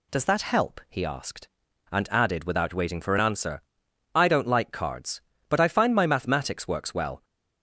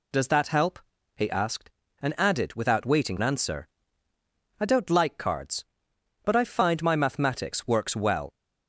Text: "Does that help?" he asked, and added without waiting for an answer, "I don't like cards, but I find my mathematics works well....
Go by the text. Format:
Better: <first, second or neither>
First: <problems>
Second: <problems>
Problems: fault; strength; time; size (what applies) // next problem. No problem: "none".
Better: first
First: none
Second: skips "for"; at 3.1 s